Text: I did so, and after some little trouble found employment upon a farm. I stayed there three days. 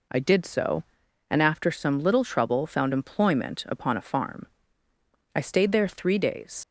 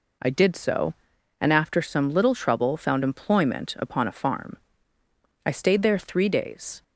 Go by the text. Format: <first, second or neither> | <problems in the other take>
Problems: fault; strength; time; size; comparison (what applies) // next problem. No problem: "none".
second | leaves "days" unfinished; at 6.6 s; 85 ms